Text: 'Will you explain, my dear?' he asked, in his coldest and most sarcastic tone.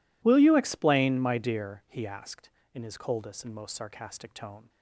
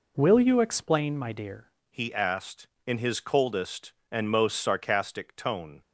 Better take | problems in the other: first | changes voice at "he"; from 1.8 s on; 4.0 s long

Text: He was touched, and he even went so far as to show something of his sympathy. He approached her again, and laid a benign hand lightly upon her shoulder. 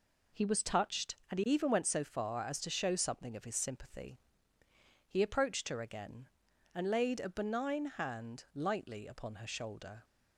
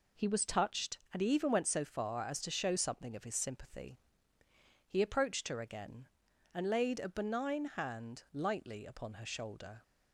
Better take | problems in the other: neither | none

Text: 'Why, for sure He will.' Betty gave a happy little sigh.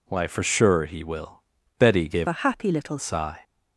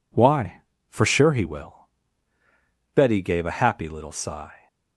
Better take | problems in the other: second | changes voice from "a" to "little"; from 2.2 to 2.9 s; 0.7 s long

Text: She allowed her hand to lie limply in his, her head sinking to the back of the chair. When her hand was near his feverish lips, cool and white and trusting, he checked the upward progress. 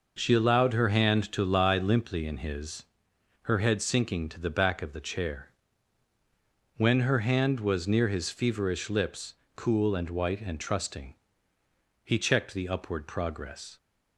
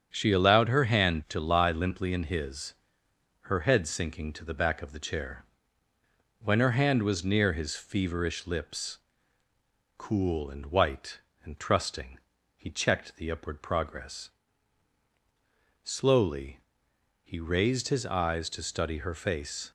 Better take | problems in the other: first | starts louder than the rest; strong; until 1.1 s; 8 dB // goes on to say "Slowly he raised his eyes to study her face"; strong; from 15.8 s on; 3.8 s long

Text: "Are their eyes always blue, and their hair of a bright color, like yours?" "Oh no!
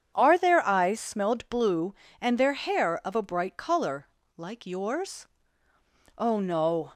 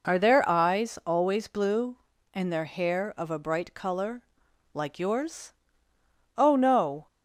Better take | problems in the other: second | starts louder than the rest; strong; until 1.1 s; 8 dB // says "smelled" for "always"; at 0.9 s

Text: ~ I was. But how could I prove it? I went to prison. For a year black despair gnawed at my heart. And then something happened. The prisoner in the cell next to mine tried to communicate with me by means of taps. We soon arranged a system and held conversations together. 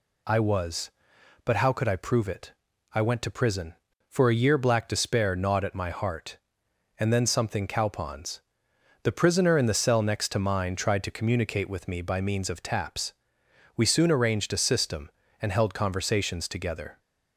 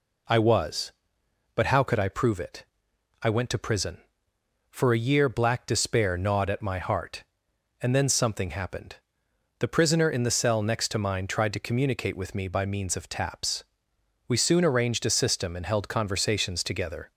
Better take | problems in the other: second | says "cowpons" for "happened"; at 7.6 s

